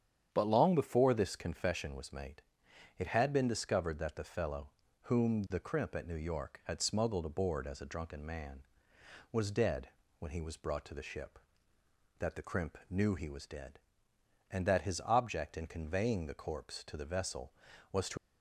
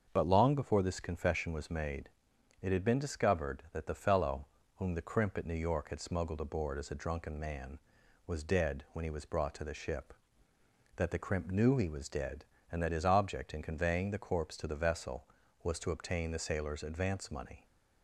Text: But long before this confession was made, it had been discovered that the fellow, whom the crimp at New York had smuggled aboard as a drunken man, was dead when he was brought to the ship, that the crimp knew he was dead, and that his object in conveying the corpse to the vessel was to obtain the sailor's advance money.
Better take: second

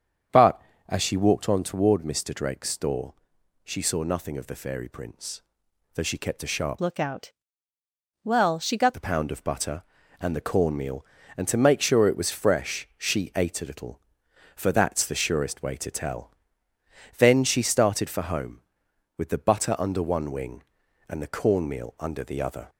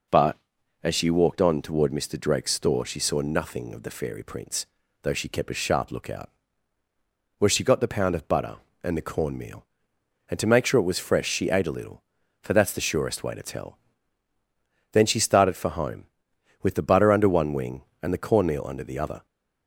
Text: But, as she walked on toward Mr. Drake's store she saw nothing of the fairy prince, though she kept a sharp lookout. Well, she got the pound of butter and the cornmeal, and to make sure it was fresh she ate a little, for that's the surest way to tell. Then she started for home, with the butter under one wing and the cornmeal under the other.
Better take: second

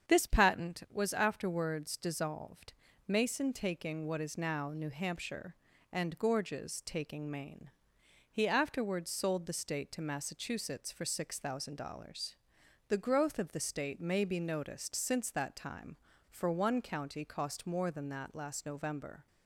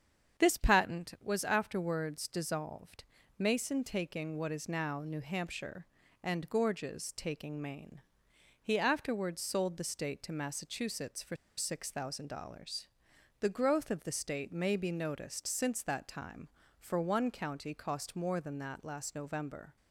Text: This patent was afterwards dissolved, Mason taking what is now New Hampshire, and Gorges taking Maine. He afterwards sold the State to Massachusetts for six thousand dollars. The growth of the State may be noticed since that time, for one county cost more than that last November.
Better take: first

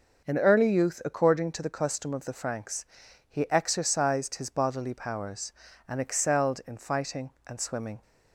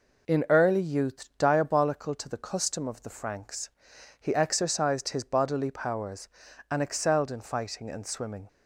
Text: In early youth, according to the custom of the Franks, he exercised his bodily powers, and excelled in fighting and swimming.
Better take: first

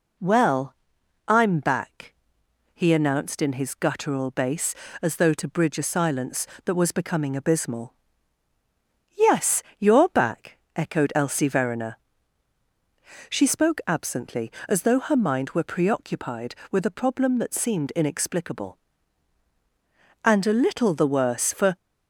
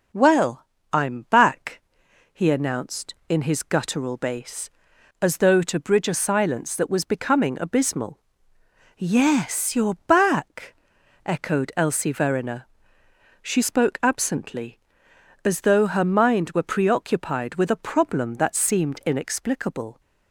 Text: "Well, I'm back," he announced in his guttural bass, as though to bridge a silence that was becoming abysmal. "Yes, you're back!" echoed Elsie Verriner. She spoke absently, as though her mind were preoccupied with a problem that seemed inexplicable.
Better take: second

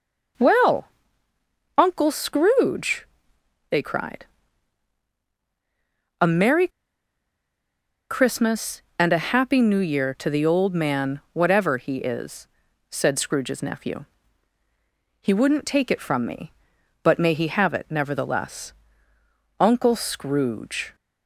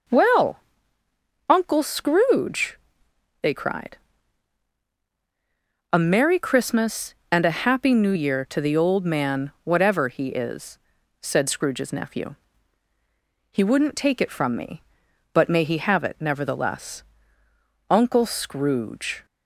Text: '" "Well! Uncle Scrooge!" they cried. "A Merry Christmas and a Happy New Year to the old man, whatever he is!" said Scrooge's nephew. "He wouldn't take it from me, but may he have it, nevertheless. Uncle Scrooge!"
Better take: second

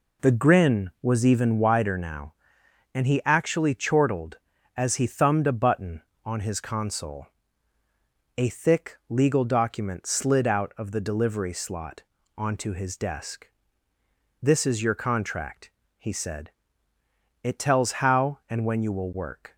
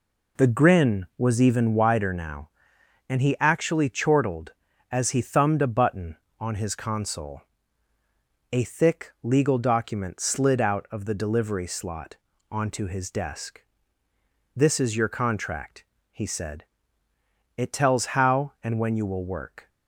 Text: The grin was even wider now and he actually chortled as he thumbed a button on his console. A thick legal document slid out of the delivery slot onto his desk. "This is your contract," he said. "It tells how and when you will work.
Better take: neither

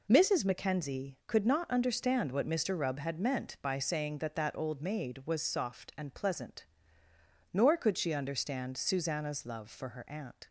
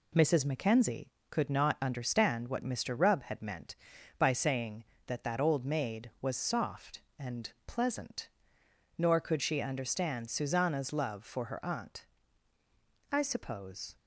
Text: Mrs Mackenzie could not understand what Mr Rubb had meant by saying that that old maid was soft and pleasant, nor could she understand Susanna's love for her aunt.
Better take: first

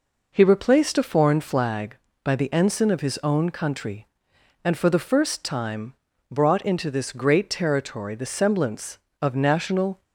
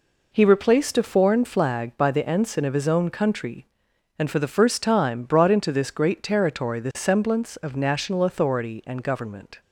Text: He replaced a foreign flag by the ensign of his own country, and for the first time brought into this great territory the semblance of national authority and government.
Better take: second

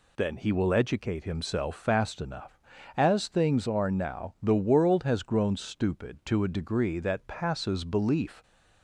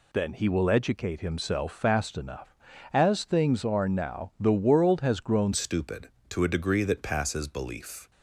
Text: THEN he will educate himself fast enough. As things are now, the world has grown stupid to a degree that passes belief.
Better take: first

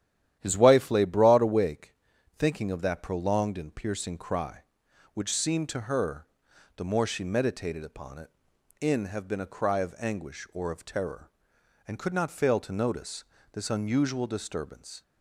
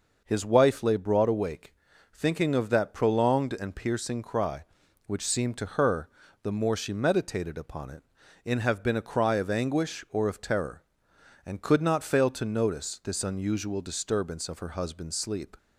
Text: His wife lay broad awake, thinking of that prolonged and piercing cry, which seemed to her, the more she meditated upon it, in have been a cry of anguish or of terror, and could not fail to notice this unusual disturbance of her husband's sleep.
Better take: second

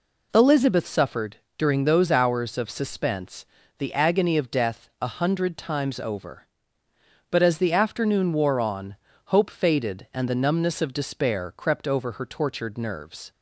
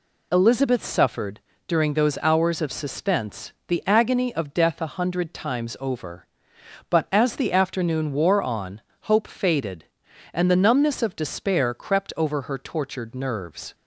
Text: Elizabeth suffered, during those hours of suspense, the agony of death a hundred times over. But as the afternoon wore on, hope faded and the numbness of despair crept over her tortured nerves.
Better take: neither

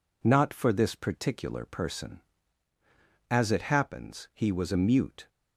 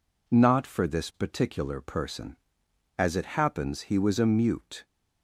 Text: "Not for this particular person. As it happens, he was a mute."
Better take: neither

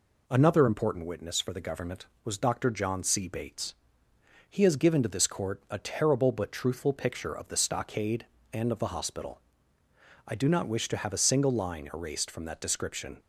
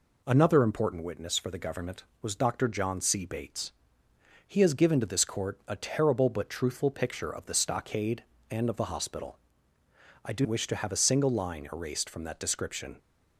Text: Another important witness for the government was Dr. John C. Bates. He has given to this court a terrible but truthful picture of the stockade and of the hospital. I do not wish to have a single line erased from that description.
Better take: first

